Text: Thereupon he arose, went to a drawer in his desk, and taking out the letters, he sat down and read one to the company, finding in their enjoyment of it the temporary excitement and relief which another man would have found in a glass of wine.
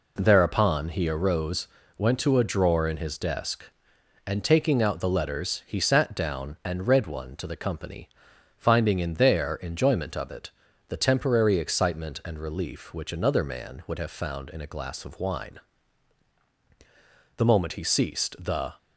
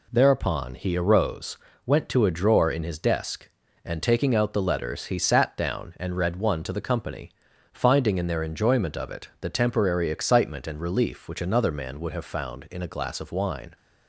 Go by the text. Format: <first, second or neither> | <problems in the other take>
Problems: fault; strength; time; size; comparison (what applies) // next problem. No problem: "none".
second | pauses between "it" and "the"; at 10.4 s; 0.40 s long // goes on to say "The moment he ceased the"; from 17.3 s on; 1.4 s long